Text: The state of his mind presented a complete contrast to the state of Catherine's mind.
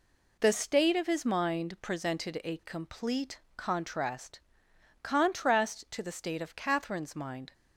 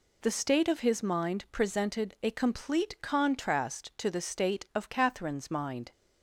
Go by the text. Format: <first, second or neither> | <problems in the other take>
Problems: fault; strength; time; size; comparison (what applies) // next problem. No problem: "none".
second | pauses between "complete" and "contrast"; slight; at 3.4 s; 0.16 s long // says "contrast" twice; at 5.0 s